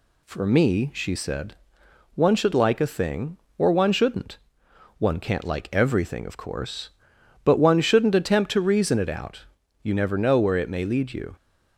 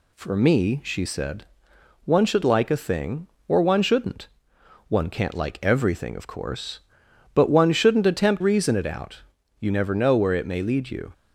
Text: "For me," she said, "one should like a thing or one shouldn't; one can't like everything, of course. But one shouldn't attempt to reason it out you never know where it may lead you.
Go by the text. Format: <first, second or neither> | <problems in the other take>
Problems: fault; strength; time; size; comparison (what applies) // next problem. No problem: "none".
first | skips "to"; at 8.4 s // pauses between "out" and "you"; at 9.1 s; 0.40 s long; also in the first